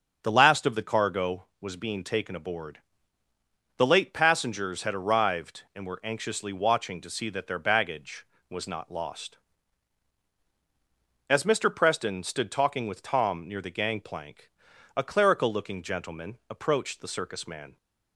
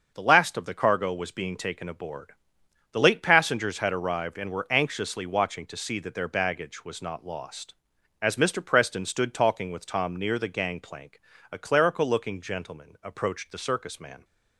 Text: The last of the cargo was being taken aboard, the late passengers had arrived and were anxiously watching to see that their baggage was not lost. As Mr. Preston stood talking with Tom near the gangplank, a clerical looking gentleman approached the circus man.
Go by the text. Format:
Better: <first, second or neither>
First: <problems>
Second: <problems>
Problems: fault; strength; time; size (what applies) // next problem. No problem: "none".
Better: neither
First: starts louder than the rest; until 1.2 s; 7 dB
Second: starts louder than the rest; until 1.1 s; 6.5 dB